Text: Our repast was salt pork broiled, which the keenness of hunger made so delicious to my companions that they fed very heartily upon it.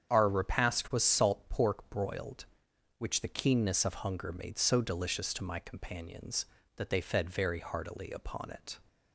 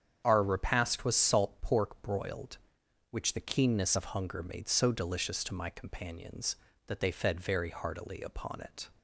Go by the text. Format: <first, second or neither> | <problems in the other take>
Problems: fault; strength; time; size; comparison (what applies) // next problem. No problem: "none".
neither | starts louder than the rest; strong; the same in both